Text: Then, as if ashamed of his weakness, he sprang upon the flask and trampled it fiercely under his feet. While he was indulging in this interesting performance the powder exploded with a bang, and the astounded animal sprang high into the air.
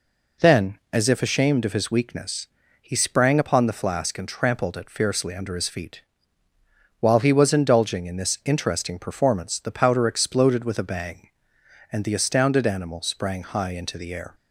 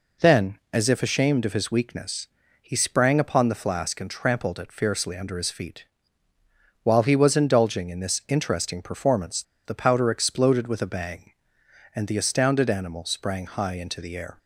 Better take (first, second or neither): first